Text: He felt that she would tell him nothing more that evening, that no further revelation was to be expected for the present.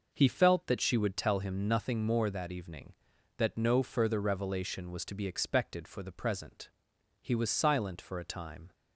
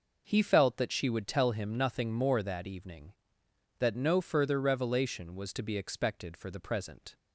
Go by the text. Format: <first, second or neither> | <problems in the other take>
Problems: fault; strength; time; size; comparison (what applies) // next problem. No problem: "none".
second | goes on to say "He was silent for a time"; from 7.2 s on; 1.5 s long